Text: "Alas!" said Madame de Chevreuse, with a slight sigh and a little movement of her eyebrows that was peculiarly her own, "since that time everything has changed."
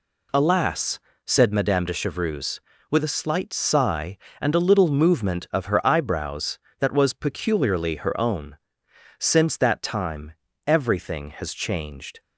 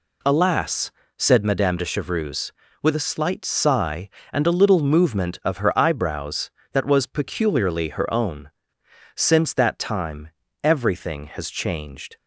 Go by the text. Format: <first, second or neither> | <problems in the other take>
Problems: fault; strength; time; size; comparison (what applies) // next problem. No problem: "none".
neither | pauses between "time" and "everything"; slight; the same in both